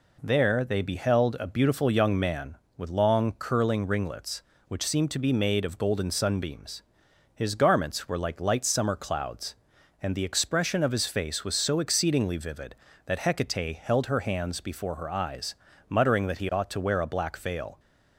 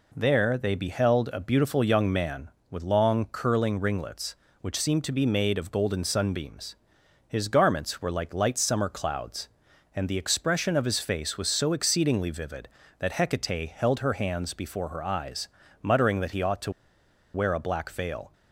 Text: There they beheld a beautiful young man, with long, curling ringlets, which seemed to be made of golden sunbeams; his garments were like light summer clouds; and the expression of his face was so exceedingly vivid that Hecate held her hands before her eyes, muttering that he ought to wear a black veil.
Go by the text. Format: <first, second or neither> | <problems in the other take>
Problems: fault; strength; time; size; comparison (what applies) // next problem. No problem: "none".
first | pauses between "to" and "wear"; noticeable; at 16.7 s; 0.63 s long